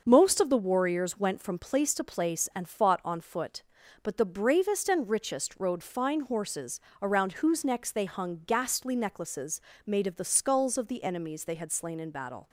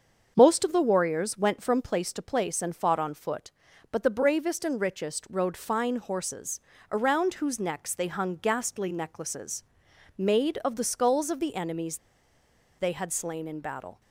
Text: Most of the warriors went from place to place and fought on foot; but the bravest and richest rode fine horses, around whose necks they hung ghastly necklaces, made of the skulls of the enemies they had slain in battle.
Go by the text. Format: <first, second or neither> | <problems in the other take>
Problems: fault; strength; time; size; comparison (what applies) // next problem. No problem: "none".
first | starts louder than the rest; until 1.3 s; 7 dB; also in the first // pauses between "enemies" and "they"; noticeable; at 11.9 s; 0.80 s long